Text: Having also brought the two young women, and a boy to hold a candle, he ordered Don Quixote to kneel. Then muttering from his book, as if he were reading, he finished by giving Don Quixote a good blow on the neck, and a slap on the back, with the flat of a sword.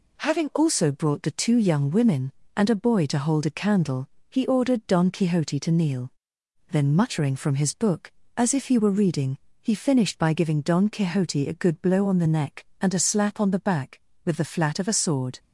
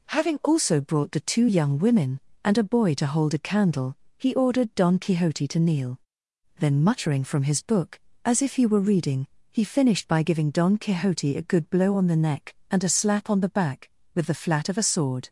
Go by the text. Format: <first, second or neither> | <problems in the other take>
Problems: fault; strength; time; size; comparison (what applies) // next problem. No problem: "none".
neither | none